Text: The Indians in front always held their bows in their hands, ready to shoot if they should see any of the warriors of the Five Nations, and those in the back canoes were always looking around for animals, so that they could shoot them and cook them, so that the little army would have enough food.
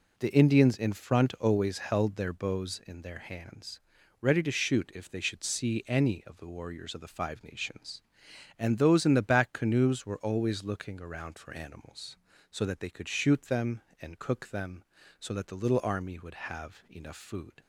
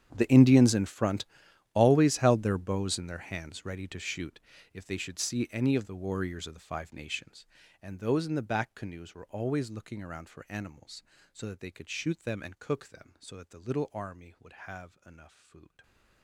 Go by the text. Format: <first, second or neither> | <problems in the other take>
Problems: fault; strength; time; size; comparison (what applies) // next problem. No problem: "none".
first | gets quieter; strong; throughout; 21.5 dB // pauses between "front" and "always"; noticeable; at 1.2 s; 0.48 s long // pauses between "shoot" and "if"; slight; at 4.4 s; 0.32 s long